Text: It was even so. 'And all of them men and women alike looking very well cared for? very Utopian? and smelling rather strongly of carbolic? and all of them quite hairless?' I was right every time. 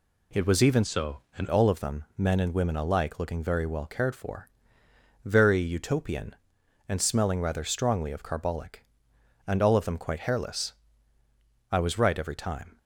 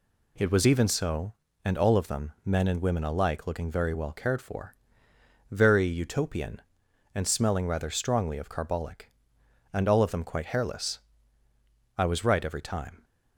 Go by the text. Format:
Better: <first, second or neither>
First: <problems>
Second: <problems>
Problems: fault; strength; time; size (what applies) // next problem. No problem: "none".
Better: second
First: changes voice from "so" to "And"; from 0.8 to 1.4 s; 0.6 s long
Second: none